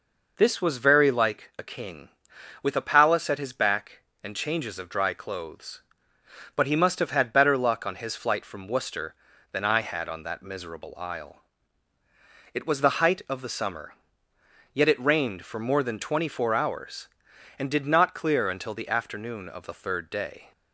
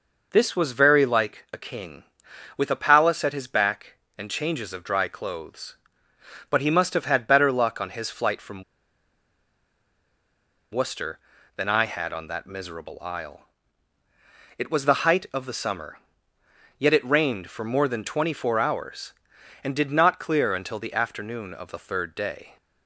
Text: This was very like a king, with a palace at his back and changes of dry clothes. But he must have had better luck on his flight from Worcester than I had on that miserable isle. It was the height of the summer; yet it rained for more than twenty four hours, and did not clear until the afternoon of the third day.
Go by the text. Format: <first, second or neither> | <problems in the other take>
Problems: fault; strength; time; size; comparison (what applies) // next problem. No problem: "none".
first | pauses between "from" and "Worcester"; strong; at 8.6 s; 2.0 s long